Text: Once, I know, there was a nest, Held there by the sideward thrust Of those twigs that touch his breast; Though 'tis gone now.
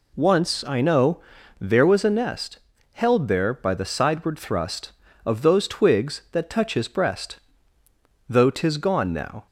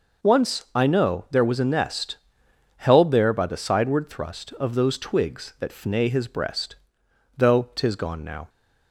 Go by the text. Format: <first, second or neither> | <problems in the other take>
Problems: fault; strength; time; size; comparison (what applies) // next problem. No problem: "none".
first | says "fnay" for "touch"; at 5.6 s